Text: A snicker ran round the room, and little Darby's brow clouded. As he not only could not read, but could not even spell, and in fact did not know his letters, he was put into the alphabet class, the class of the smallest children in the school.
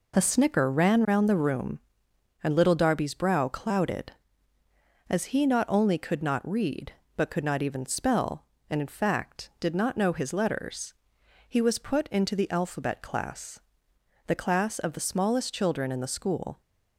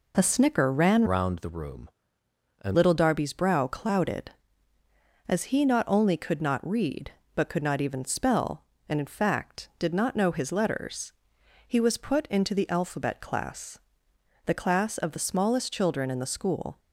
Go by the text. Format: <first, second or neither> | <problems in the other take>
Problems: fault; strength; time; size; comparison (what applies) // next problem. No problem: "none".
first | changes voice from "round" to "and"; from 1.0 to 2.7 s; 1.7 s long